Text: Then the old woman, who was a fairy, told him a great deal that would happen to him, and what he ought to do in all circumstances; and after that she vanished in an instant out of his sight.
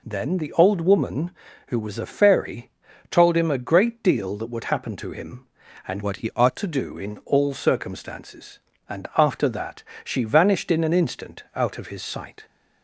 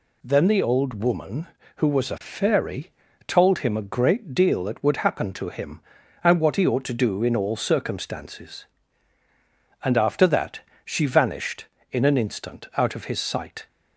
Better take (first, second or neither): second